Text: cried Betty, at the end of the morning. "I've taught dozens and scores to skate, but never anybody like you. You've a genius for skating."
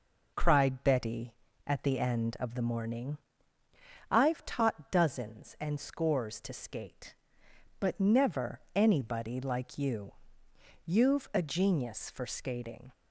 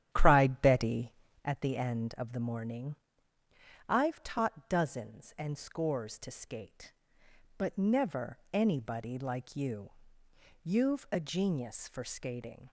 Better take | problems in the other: first | starts louder than the rest; strong; until 1.5 s; 10.5 dB

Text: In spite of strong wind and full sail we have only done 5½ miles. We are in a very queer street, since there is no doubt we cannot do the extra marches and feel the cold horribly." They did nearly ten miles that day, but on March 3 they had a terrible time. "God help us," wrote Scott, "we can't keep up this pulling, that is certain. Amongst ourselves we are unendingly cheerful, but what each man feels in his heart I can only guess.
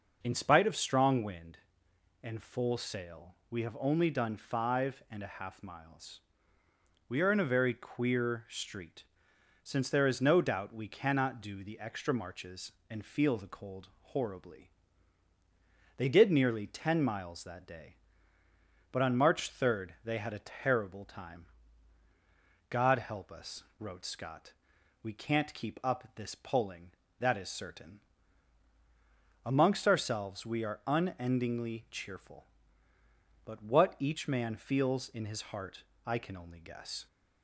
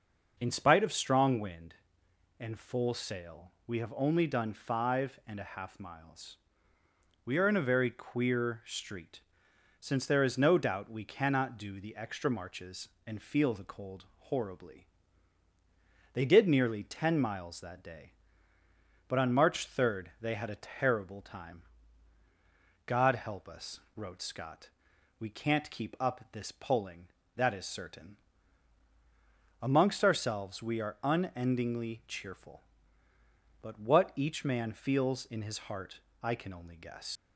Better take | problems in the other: first | pauses between "heart" and "I"; slight; at 35.9 s; 0.22 s long; slight in the first // leaves "guess" unfinished; at 37.1 s; 80 ms

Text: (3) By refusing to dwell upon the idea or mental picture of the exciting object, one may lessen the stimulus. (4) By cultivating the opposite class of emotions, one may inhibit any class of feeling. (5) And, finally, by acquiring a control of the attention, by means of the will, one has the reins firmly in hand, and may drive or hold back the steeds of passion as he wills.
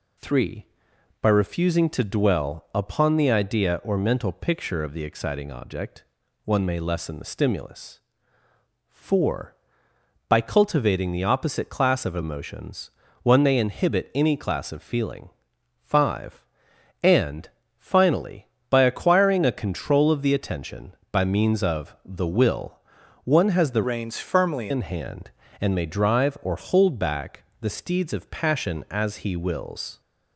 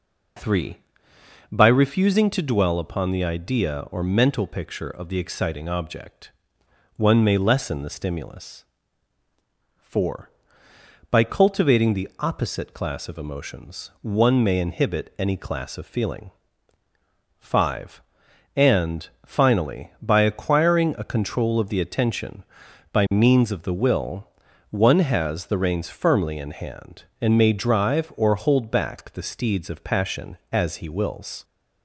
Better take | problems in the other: second | changes voice from "reins" to "firmly"; from 23.8 to 24.6 s; 0.8 s long // pauses between "back" and "the"; slight; at 27.4 s; 0.18 s long

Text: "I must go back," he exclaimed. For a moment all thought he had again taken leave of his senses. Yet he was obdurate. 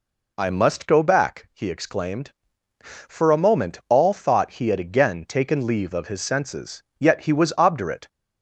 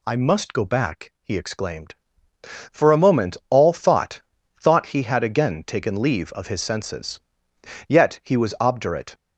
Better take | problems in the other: first | says "thought" twice; at 4.5 s

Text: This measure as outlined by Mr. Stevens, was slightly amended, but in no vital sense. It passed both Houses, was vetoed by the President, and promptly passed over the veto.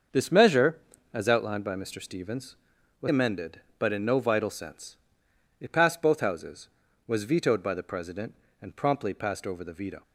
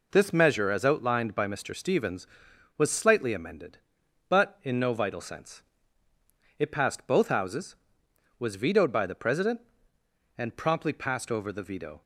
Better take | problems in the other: second | starts louder than the rest; until 1.4 s; 6.5 dB // skips "slightly"; at 3.0 s

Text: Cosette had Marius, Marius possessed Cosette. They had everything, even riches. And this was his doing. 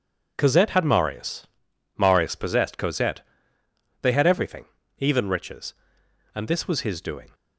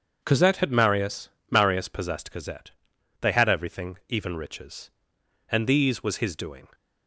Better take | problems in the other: first | starts louder than the rest; until 1.2 s; 7 dB // says "these" for "this"; at 5.6 s

